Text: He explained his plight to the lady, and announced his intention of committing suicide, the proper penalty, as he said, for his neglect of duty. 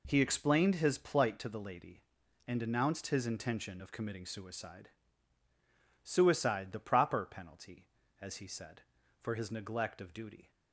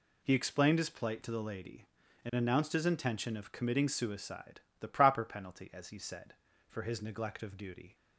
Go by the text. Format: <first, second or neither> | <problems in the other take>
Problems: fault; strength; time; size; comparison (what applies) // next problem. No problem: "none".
second | says "suicide" twice; at 6.0 s